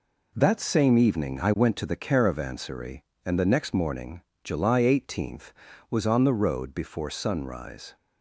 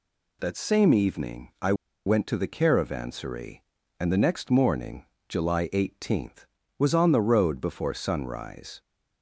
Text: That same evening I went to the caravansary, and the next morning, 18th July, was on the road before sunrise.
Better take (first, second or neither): first